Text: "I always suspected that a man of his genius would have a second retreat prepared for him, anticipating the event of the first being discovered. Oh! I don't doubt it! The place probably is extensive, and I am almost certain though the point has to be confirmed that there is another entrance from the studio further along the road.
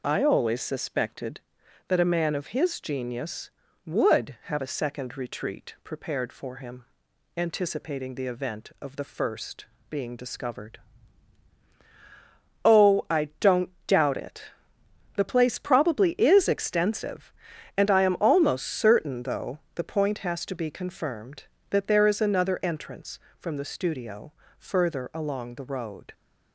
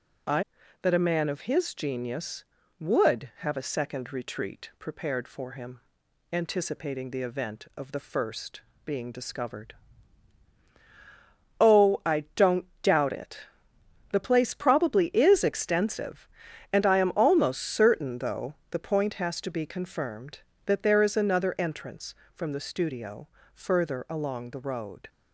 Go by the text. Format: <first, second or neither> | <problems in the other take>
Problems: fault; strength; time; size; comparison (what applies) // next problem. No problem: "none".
first | skips "always suspected"; at 0.6 s // pauses between "first" and "being"; slight; at 8.6 s; 0.24 s long; slight in the first // pauses between "don't" and "doubt"; slight; at 12.6 s; 0.16 s long; slight in the first // pauses between "though" and "the"; slight; at 18.5 s; 0.16 s long; slight in the first // pauses between "studio" and "further"; slight; at 23.2 s; 0.28 s long; slight in the first